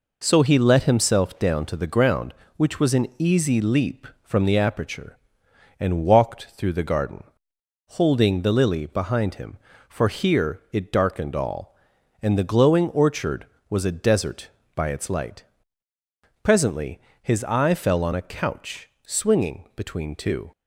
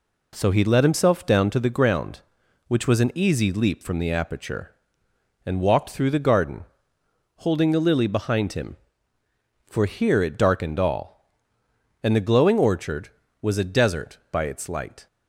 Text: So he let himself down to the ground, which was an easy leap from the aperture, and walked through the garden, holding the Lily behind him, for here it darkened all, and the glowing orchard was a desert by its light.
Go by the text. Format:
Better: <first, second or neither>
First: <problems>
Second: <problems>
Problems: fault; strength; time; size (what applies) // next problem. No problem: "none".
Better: second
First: goes on to say "Presently his eye fell on a couch swinging between two"; strong; from 16.4 s on; 4.0 s long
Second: none